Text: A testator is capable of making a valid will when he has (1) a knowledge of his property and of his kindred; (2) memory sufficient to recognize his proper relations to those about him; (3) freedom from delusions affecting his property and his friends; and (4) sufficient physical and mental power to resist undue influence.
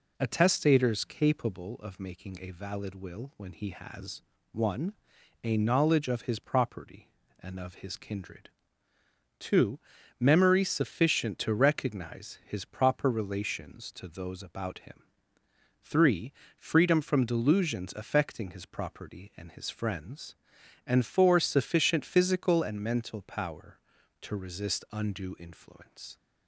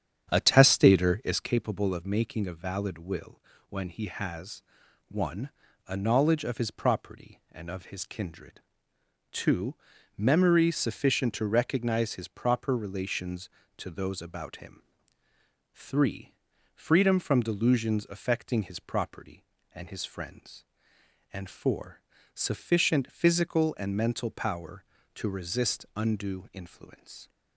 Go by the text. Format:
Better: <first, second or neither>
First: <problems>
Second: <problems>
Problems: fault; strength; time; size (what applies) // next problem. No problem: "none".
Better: first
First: none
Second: starts louder than the rest; strong; until 1.7 s; 8.5 dB // pauses between "will" and "when"; slight; at 3.3 s; 0.30 s long